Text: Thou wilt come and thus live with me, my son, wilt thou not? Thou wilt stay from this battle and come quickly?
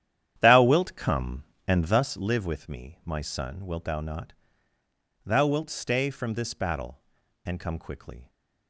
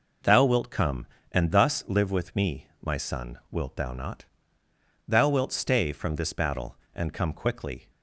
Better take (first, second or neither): second